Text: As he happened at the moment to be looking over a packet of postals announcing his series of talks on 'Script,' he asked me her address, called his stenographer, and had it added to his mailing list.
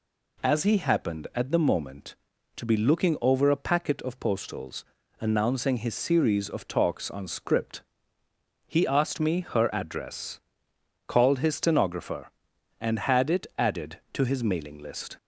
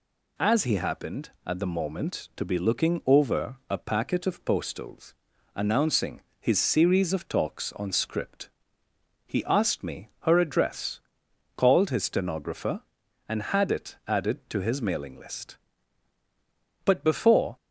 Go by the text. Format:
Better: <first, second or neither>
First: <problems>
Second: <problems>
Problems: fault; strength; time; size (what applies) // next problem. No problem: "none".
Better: first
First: pauses between "postals" and "announcing"; slight; at 4.8 s; 0.34 s long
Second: pauses between "postals" and "announcing"; at 5.1 s; 0.40 s long // pauses between "announcing" and "his"; slight; at 6.2 s; 0.18 s long // goes on to say "But before"; noticeable; from 16.8 s on; 0.72 s long